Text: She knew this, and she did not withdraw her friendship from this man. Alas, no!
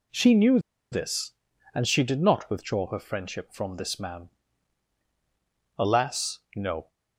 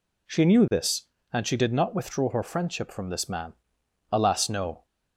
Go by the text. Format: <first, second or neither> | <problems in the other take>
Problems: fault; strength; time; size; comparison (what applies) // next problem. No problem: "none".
second | pauses between "knew" and "this"; slight; at 0.5 s; 0.33 s long